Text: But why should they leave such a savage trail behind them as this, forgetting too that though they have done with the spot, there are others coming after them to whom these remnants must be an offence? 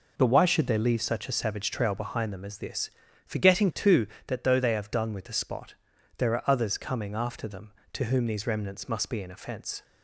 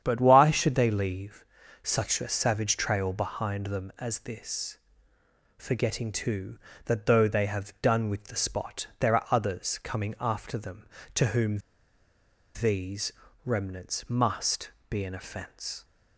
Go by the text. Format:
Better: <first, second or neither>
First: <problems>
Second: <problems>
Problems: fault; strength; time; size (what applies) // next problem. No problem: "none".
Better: first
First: none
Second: starts louder than the rest; strong; until 1.0 s; 9 dB // pauses between "leave" and "such"; at 1.4 s; 0.40 s long // pauses between "whom" and "these"; noticeable; at 11.5 s; 0.96 s long // pauses between "these" and "remnants"; slight; at 13.1 s; 0.32 s long // pauses between "must" and "be"; slight; at 14.7 s; 0.18 s long